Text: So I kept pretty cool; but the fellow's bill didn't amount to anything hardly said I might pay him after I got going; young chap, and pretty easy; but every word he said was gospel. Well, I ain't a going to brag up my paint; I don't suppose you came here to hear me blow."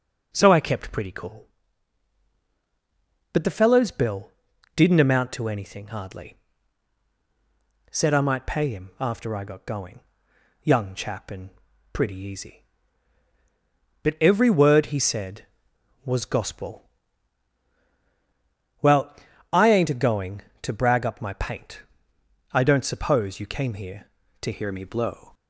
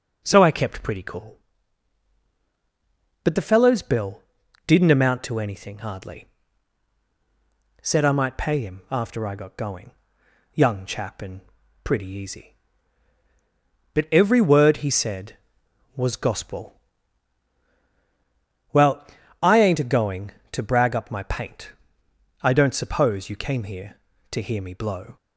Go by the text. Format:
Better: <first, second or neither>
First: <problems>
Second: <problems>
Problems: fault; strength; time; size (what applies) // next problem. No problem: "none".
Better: second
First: pauses between "bill" and "didn't"; at 4.3 s; 0.44 s long // pauses between "hardly" and "said"; strong; at 6.3 s; 1.5 s long // pauses between "and" and "pretty"; at 11.5 s; 0.42 s long // changes voice at "hear"; from 24.5 s on; 0.8 s long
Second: pauses between "bill" and "didn't"; at 4.2 s; 0.44 s long // pauses between "hardly" and "said"; strong; at 6.2 s; 1.5 s long // pauses between "and" and "pretty"; at 11.4 s; 0.42 s long